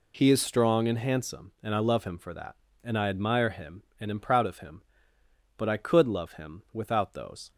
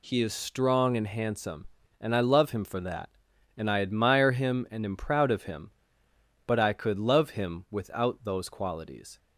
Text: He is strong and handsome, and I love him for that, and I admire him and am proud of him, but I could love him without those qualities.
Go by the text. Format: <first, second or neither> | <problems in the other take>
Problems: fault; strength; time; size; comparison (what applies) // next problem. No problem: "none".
second | stops before "qualities"; at 7.5 s